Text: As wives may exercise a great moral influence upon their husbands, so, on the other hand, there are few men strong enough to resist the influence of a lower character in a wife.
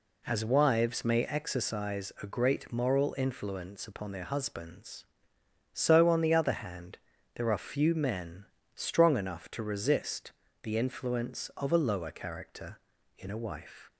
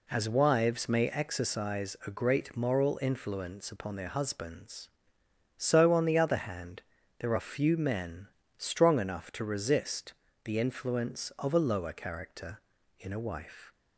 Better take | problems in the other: neither | pauses between "men" and "strong"; slight; the same in both // pauses between "resist" and "the"; slight; the same in both

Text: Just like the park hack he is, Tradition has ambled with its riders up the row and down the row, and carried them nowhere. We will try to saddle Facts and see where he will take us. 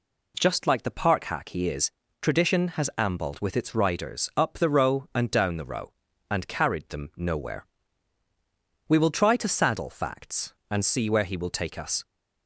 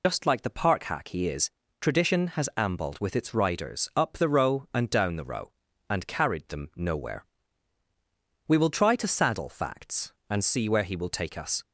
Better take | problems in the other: first | loses the start of "Just"; at 0.0 s; 110 ms

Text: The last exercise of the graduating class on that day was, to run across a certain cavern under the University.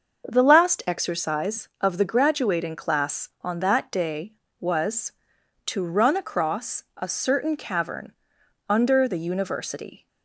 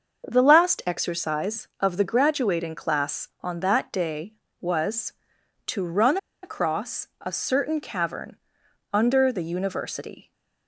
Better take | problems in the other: first | starts louder than the rest; until 1.3 s; 6.5 dB; also in the first // pauses between "run" and "across"; slight; at 6.1 s; 0.26 s long // pauses between "cavern" and "under"; noticeable; at 8.3 s; 0.52 s long; noticeable in the first

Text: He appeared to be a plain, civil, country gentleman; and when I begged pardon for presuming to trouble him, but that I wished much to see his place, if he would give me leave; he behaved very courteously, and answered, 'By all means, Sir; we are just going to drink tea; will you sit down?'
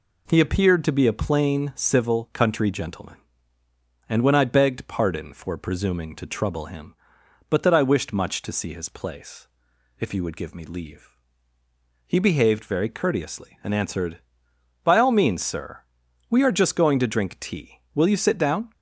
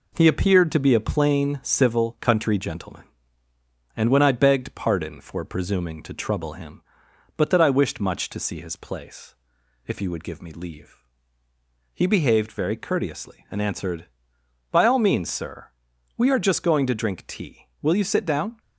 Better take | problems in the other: first | gets quieter; slight; throughout; 3.5 dB

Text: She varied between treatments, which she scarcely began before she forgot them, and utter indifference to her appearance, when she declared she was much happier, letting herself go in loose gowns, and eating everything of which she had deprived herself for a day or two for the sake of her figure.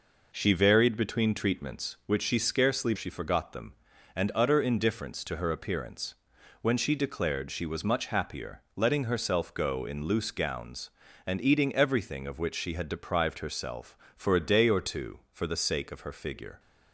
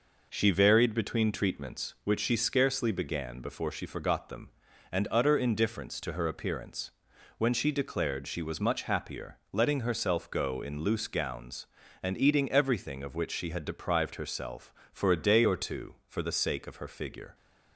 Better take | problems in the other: second | skips "began before"; at 2.9 s

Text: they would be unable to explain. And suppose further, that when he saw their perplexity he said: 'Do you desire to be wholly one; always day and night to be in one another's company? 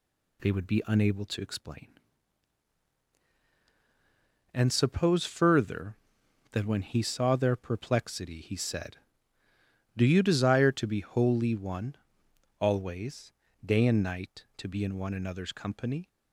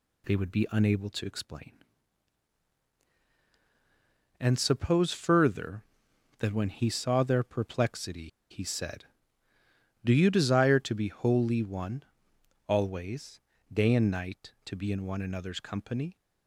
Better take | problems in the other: first | pauses between "perplexity" and "he"; slight; at 8.2 s; 0.23 s long // pauses between "always" and "day"; slight; at 13.3 s; 0.32 s long; slight in the first

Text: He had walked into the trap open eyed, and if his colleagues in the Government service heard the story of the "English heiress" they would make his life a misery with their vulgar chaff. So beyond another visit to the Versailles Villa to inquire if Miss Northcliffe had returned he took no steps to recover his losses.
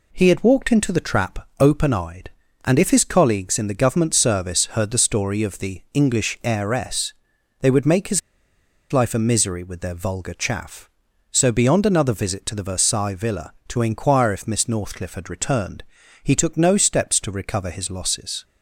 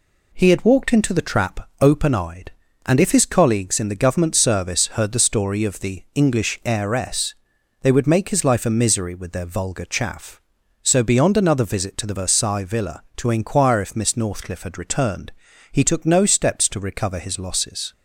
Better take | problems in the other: second | pauses between "heiress" and "they"; noticeable; at 7.1 s; 0.48 s long; noticeable in the second // pauses between "his" and "life"; noticeable; at 8.2 s; 0.71 s long // pauses between "returned" and "he"; at 15.8 s; 0.40 s long; also in the second

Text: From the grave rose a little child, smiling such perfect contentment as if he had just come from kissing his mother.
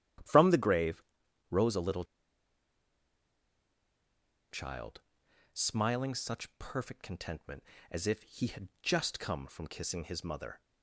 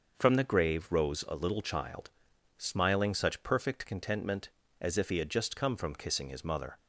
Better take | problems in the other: second | starts louder than the rest; strong; until 1.7 s; 11.5 dB; also in the second // pauses between "grave" and "rose"; noticeable; at 1.0 s; 0.46 s long // pauses between "little" and "child"; strong; at 2.0 s; 2.4 s long

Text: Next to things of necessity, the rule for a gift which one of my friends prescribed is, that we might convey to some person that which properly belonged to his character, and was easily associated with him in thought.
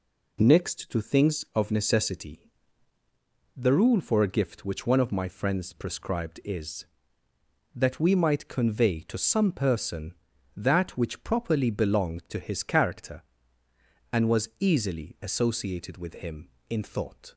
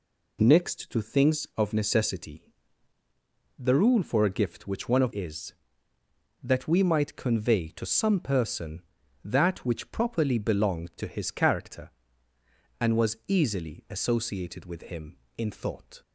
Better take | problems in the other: first | skips "my friends prescribed"; at 5.1 s

